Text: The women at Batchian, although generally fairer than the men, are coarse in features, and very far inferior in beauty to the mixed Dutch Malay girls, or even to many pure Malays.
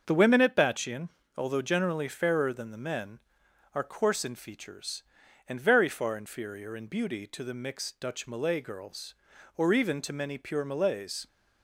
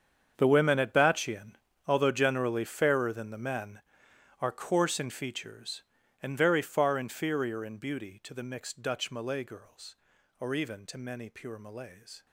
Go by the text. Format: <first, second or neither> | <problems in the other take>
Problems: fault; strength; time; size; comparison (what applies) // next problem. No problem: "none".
first | gets quieter; strong; throughout; 16 dB // starts louder than the rest; strong; until 1.3 s; 7.5 dB; also in the first